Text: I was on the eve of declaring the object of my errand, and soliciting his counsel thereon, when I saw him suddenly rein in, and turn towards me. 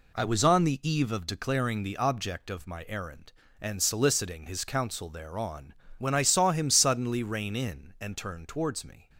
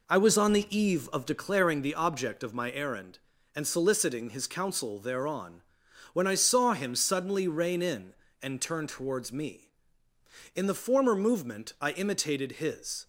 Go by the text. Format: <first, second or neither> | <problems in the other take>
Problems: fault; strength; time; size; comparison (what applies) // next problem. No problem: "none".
first | goes on to say "In the former movement I imitated his"; strong; from 10.5 s on; 2.5 s long